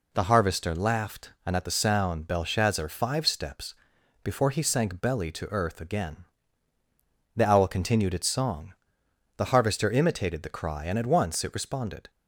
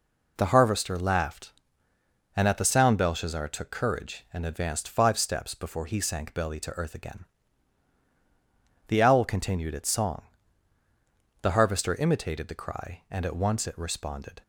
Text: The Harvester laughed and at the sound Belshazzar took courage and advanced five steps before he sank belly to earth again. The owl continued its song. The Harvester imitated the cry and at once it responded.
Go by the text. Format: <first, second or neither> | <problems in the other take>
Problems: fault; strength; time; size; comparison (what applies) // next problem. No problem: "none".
second | skips "took courage and advanced"; at 2.8 s // pauses between "steps" and "before"; noticeable; at 3.7 s; 0.50 s long